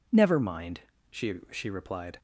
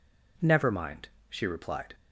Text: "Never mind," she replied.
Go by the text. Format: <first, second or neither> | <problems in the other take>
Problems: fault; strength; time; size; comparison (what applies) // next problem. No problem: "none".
second | says "she" twice; at 1.5 s